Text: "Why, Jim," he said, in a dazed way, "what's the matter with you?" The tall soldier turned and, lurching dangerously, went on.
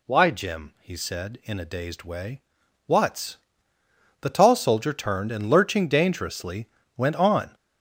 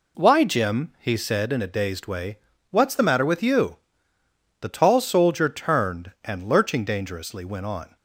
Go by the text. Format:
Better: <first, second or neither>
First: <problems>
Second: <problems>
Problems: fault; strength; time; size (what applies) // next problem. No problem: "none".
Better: second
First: skips "the matter with you"; at 3.7 s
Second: none